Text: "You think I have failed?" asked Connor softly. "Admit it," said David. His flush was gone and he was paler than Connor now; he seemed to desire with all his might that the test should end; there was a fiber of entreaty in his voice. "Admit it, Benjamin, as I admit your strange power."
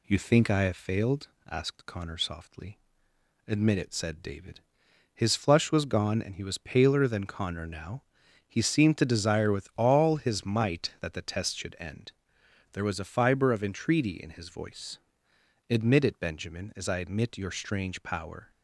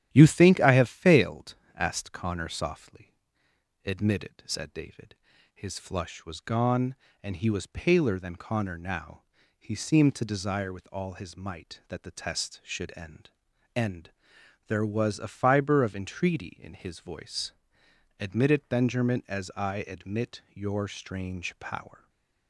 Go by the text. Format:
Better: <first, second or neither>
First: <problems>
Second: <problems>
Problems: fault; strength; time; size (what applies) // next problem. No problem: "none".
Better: first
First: none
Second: starts louder than the rest; strong; until 1.1 s; 11 dB // says "end" twice; at 13.7 s // stays silent after the last word; slight; from 21.9 s on; 0.5 s long